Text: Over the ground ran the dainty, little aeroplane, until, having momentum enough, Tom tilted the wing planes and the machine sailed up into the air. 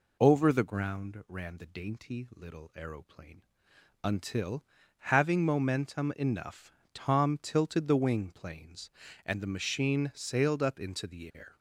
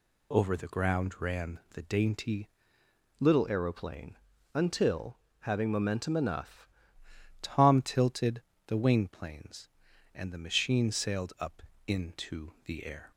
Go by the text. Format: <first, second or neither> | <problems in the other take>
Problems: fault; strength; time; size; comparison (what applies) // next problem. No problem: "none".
first | changes voice from "little" to "enough"; from 3.1 to 6.6 s; 3.5 s long // pauses between "tilted" and "the"; slight; at 8.4 s; 0.26 s long // pauses between "up" and "into"; slight; at 11.6 s; 0.26 s long